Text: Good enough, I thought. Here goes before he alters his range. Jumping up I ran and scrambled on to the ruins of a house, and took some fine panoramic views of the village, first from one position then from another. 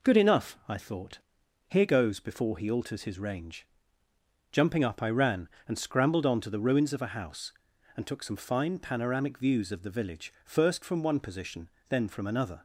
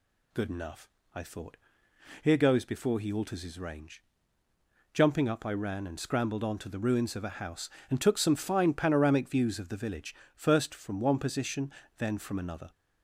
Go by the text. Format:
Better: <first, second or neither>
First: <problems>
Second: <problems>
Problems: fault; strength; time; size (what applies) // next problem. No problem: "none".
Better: neither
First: pauses between "position" and "then"; slight; at 11.6 s; 0.22 s long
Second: pauses between "position" and "then"; slight; at 11.7 s; 0.28 s long